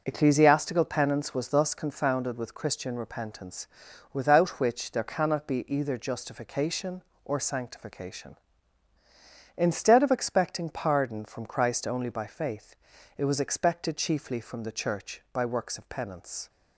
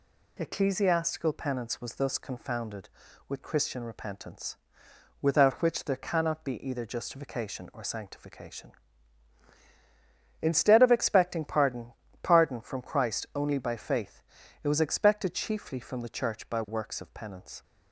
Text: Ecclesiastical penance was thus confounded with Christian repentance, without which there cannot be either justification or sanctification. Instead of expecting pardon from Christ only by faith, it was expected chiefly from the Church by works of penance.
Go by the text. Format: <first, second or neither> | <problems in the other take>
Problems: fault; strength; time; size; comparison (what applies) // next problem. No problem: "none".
first | says "pardon" twice; at 12.2 s